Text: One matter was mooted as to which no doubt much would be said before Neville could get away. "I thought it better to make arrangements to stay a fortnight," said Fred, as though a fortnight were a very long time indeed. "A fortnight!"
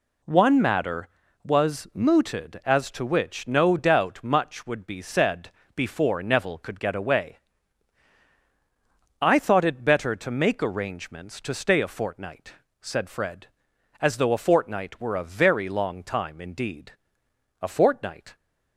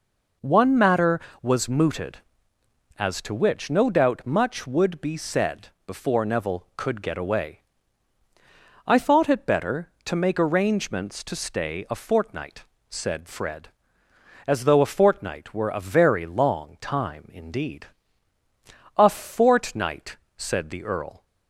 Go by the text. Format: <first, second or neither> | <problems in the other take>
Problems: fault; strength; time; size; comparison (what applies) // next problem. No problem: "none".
first | pauses between "said" and "before"; slight; at 5.6 s; 0.18 s long; slight in the first // goes on to say "said the Earl"; noticeable; from 20.3 s on; 0.88 s long